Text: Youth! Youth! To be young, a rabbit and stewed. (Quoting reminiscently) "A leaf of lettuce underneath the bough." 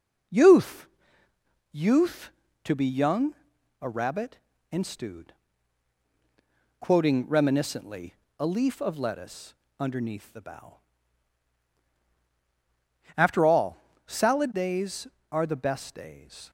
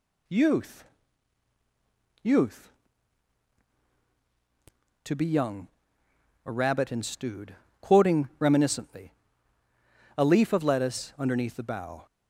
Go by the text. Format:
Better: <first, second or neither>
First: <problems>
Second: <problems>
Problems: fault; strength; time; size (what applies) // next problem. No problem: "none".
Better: second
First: pauses between "lettuce" and "underneath"; slight; at 9.5 s; 0.26 s long // goes on to say "After all salad days are the best days"; strong; from 13.1 s on; 3.3 s long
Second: none